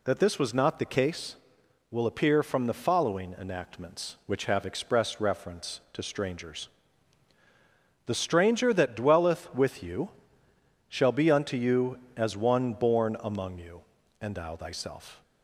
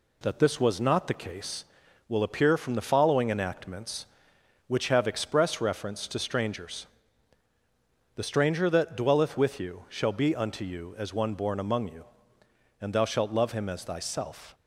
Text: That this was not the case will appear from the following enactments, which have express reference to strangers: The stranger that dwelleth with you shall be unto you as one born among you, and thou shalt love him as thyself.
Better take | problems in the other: second | pauses between "you" and "shall"; noticeable; at 10.1 s; 0.80 s long // skips "shalt love him as"; at 14.5 s

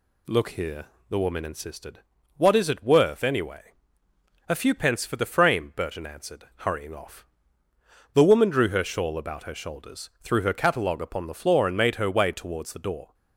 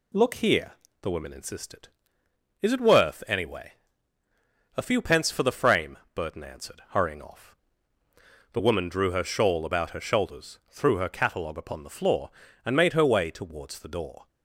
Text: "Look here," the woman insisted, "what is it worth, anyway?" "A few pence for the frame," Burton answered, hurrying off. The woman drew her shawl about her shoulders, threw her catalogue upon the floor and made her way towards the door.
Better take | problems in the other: first | skips "what"; at 2.2 s

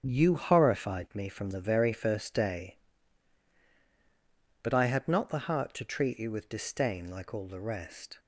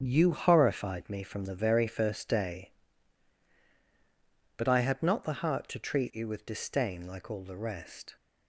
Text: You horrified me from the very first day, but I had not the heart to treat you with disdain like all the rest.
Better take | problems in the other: neither | starts louder than the rest; strong; the same in both

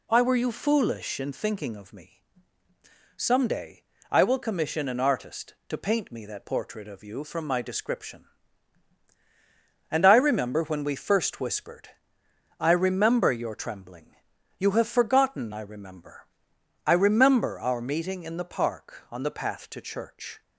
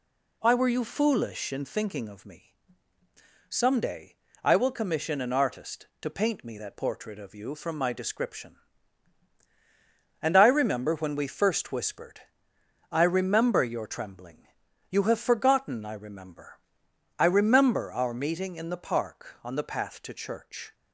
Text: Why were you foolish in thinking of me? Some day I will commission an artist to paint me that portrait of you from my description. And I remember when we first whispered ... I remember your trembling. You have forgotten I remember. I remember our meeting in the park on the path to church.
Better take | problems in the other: neither | pauses between "day" and "I"; slight; the same in both

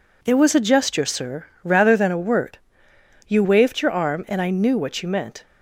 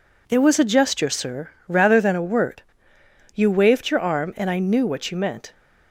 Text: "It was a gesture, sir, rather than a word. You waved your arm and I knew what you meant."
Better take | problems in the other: neither | none

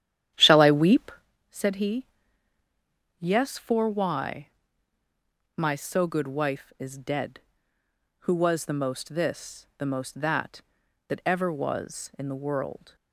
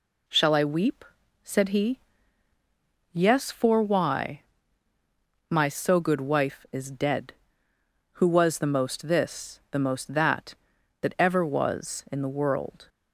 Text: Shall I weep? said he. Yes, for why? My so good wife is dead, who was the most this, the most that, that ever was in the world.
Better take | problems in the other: second | starts louder than the rest; strong; until 1.3 s; 11 dB

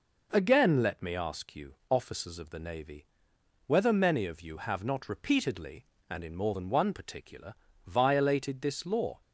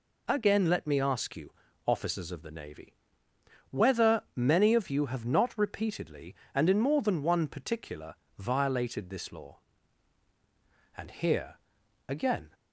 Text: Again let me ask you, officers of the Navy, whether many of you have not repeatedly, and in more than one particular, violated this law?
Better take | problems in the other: first | goes on to say "And here again"; from 10.9 s on; 1.5 s long

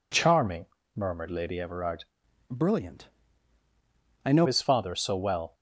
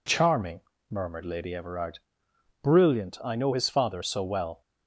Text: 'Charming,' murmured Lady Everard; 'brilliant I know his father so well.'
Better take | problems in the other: second | changes voice from "brilliant" to "know"; from 2.4 to 4.4 s; 2.0 s long // pauses between "brilliant" and "I"; at 3.0 s; 1.1 s long

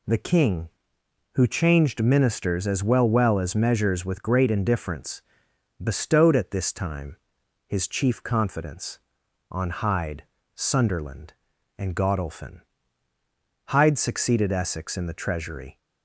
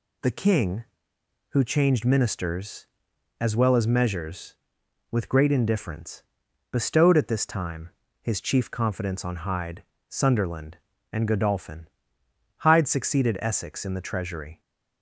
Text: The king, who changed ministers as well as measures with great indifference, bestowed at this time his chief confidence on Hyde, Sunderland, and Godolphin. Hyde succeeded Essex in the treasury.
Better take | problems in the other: second | says "well" twice; at 3.0 s // pauses between "time" and "his"; noticeable; at 7.1 s; 0.50 s long; slight in the second

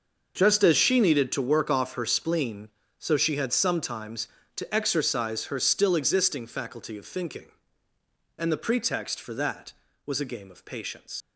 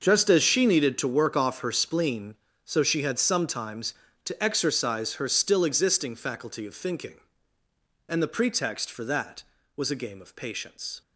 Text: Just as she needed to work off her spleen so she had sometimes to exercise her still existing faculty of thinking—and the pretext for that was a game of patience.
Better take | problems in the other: second | starts louder than the rest; noticeable; until 1.3 s; 6 dB; noticeable in the second // leaves "patience" unfinished; at 11.2 s; 100 ms

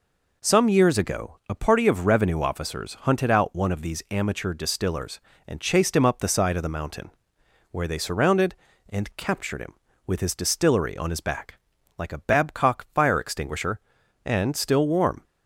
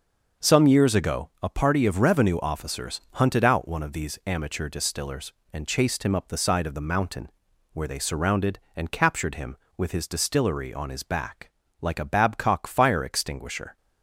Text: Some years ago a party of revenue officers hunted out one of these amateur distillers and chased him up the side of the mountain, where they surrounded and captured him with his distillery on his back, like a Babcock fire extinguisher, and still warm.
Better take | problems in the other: first | starts louder than the rest; until 1.5 s; 6 dB // stops before "and still warm"; at 13.7 s

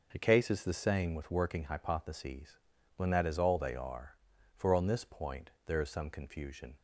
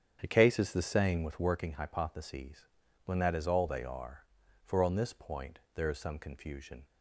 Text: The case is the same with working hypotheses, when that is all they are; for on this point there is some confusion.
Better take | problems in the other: first | starts louder than the rest; strong; until 1.6 s; 8 dB // pauses between "point" and "there"; slight; at 5.5 s; 0.16 s long; slight in the first

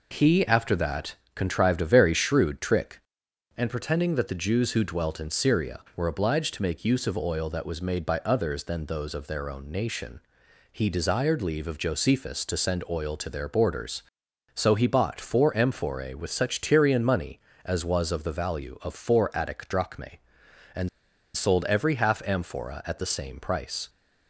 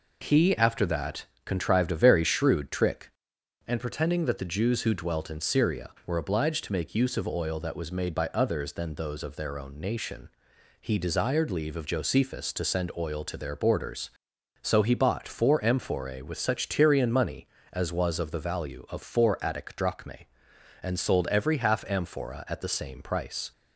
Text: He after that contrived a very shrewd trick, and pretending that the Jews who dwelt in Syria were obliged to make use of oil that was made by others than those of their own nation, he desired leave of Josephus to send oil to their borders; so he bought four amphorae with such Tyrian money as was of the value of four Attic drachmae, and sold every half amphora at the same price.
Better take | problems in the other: second | pauses between "that" and "contrived"; slight; at 1.1 s; 0.20 s long; slight in the second // pauses between "and" and "sold"; noticeable; at 20.8 s; 0.47 s long

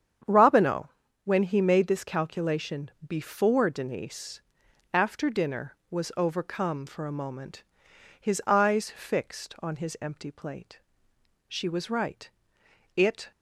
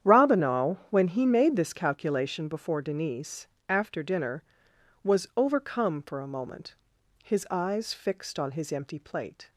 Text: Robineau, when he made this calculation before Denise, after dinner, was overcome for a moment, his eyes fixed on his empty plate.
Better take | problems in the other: second | starts louder than the rest; strong; until 1.6 s; 8.5 dB; strong in the second // pauses between "calculation" and "before"; slight; at 2.9 s; 0.16 s long // goes on to say "She was right it"; strong; from 11.5 s on; 1.8 s long

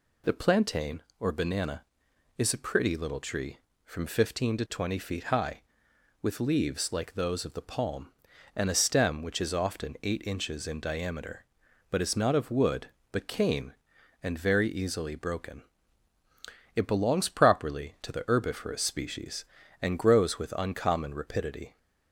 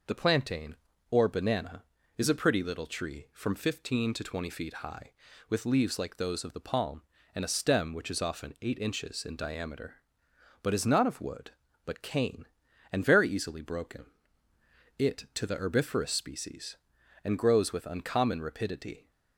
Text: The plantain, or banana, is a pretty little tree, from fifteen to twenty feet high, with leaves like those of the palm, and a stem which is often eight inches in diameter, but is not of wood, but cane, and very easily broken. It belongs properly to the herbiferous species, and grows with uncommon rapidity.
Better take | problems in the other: first | skips "belongs properly"; at 15.2 s

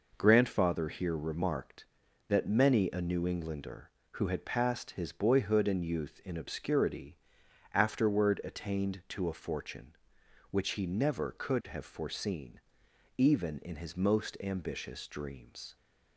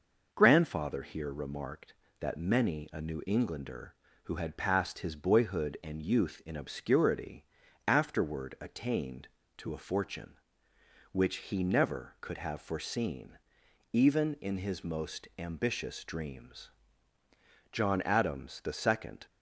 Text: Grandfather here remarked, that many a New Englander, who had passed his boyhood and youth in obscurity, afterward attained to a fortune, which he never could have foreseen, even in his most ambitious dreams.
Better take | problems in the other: first | goes on to say "John Adams the second"; from 17.7 s on; 1.5 s long

